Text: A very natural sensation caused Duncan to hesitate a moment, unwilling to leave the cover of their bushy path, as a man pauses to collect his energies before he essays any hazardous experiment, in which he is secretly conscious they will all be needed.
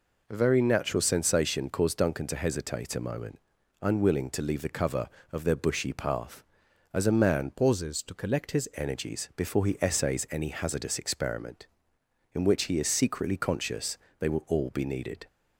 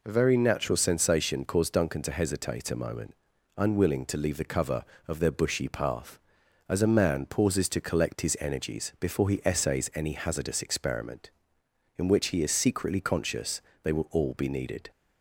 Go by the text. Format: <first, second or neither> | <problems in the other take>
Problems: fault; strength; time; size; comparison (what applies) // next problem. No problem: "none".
second | changes voice from "pauses" to "his"; from 7.5 to 8.6 s; 1.1 s long // pauses between "conscious" and "they"; slight; at 13.9 s; 0.22 s long; slight in the second